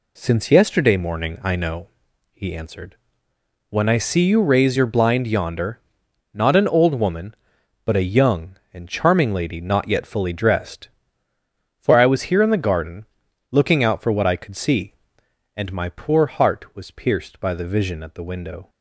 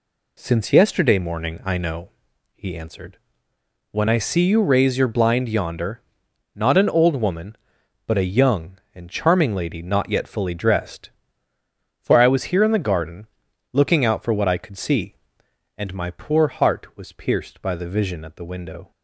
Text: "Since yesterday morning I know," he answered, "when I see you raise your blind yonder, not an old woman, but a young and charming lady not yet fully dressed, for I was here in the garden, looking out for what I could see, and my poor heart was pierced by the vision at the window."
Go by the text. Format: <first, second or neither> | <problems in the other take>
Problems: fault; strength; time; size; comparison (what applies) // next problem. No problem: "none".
neither | none